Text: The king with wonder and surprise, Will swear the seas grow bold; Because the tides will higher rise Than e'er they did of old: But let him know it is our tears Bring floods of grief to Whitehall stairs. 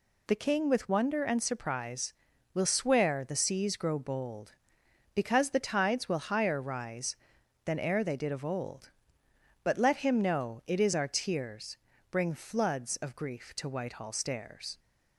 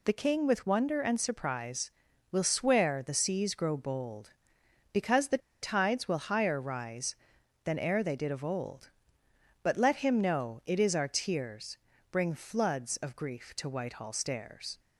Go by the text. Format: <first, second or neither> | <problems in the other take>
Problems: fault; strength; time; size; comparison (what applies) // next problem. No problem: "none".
first | pauses between "the" and "tides"; slight; at 5.3 s; 0.24 s long // pauses between "tears" and "Bring"; slight; at 11.7 s; 0.34 s long; slight in the first